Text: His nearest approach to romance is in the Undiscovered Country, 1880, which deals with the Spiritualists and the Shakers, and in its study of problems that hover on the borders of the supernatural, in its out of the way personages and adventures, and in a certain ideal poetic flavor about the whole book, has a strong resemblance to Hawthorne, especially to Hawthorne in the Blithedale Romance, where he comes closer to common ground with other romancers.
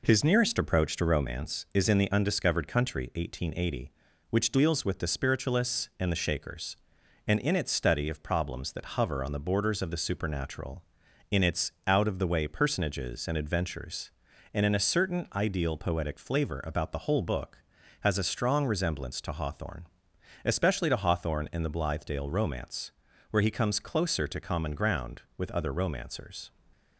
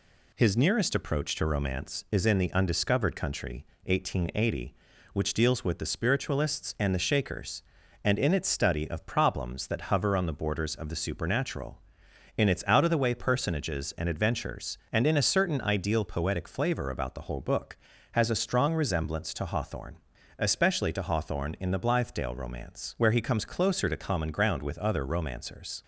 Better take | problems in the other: neither | none

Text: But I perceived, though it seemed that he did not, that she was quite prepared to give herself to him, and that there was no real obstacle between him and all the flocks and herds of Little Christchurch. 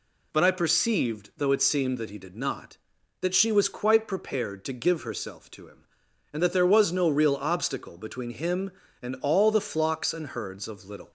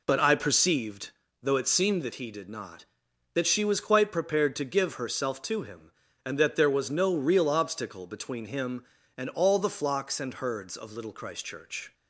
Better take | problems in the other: second | stops before "Christchurch"; at 11.0 s

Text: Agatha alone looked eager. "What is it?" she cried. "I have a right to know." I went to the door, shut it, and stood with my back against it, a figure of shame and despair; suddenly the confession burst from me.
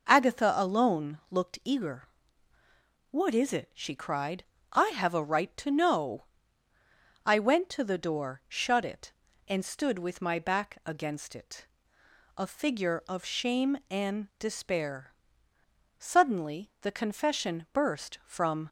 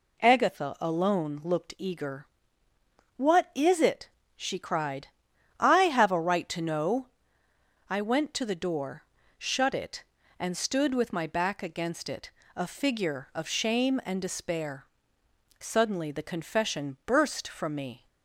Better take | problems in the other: second | stops before "me"; at 18.6 s

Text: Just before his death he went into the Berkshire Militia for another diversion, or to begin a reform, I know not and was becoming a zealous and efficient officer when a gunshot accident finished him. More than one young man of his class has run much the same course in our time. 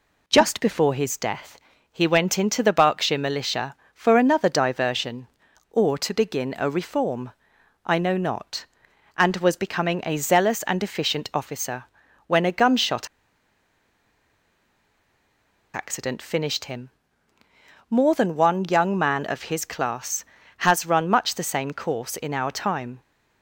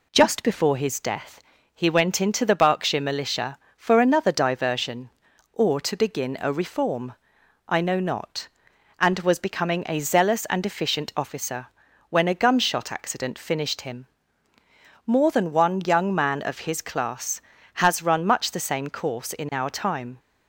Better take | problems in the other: second | pauses between "death" and "he"; slight; at 1.5 s; 0.34 s long; slight in the second // pauses between "officer" and "when"; at 11.8 s; 0.42 s long; also in the second // pauses between "gunshot" and "accident"; strong; at 13.0 s; 2.6 s long

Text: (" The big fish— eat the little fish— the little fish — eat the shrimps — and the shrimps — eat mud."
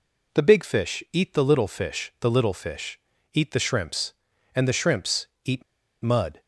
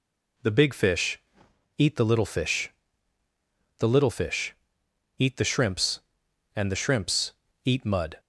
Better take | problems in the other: second | pauses between "eat" and "mud"; at 5.6 s; 0.41 s long

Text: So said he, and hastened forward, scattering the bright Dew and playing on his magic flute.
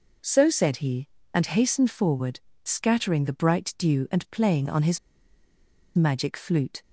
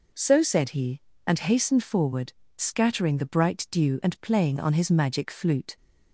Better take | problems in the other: second | pauses between "his" and "magic"; noticeable; at 4.9 s; 0.97 s long

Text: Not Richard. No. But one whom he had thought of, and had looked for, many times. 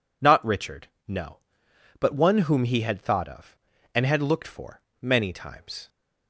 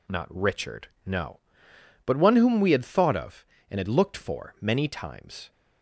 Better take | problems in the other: first | says "we" for "he"; at 2.6 s

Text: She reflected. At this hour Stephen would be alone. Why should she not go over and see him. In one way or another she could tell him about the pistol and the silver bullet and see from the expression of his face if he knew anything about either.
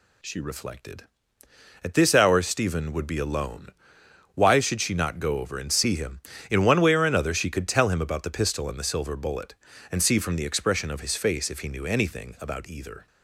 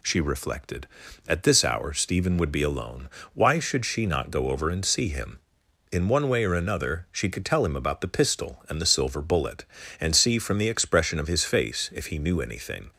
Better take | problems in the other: first | stops before "about either"; at 12.9 s

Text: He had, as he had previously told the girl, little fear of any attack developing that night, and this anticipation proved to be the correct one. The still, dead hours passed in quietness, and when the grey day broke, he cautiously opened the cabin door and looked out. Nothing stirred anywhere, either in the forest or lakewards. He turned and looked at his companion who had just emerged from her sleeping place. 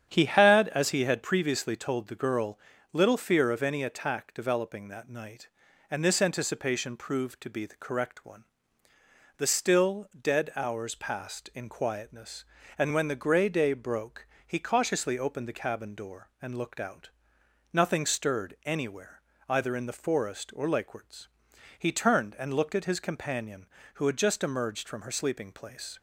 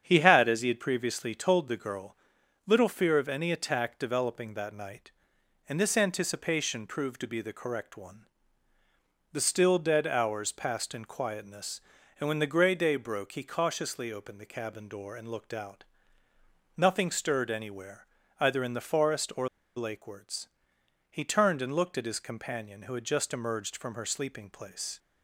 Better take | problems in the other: first | starts louder than the rest; strong; until 1.0 s; 8 dB; strong in the first // pauses between "or" and "lakewards"; slight; at 19.4 s; 0.28 s long

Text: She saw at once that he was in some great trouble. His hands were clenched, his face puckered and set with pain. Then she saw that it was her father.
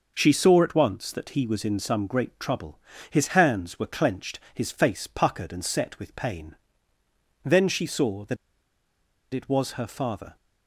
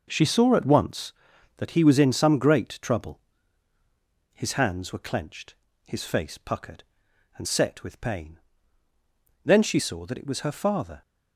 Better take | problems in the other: second | pauses between "that" and "it"; noticeable; at 8.3 s; 0.97 s long

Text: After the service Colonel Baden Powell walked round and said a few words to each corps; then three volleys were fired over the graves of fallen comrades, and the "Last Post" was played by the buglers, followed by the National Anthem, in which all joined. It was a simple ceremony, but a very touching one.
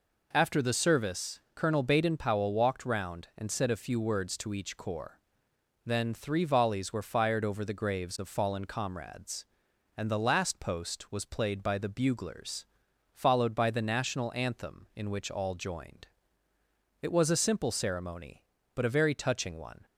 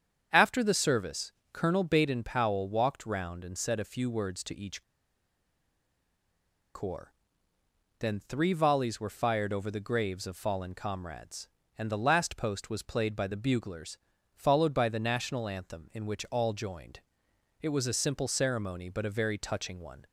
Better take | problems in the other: first | starts louder than the rest; strong; until 1.5 s; 8 dB // pauses between "service" and "Colonel"; slight; at 1.3 s; 0.22 s long // pauses between "each" and "corps"; strong; at 4.8 s; 1.9 s long

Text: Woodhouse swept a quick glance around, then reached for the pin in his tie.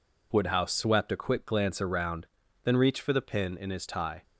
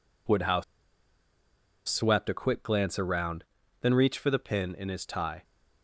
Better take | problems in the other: first | pauses between "Woodhouse" and "swept"; strong; at 0.6 s; 1.2 s long

